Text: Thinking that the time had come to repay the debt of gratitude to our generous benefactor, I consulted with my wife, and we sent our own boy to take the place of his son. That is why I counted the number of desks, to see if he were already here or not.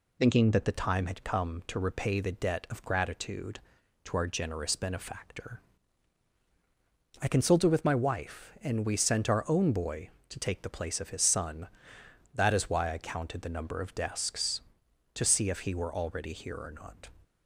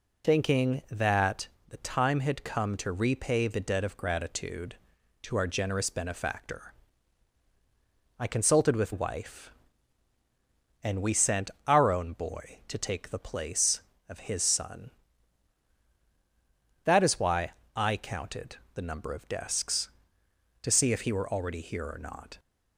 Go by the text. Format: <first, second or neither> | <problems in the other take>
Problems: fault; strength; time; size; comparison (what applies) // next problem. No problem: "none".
first | pauses between "that" and "the"; slight; at 1.4 s; 0.24 s long // skips "my"; at 8.9 s // pauses between "sent" and "our"; slight; at 11.5 s; 0.16 s long // pauses between "why" and "I"; slight; at 17.5 s; 0.24 s long // pauses between "counted" and "the"; slight; at 18.5 s; 0.20 s long